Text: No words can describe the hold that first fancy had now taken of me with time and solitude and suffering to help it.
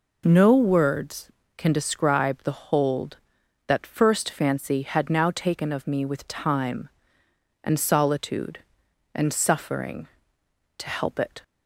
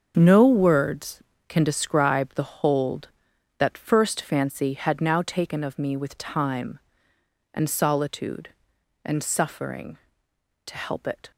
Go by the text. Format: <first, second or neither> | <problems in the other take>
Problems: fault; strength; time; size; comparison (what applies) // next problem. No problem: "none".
first | gets quieter; strong; throughout; 11 dB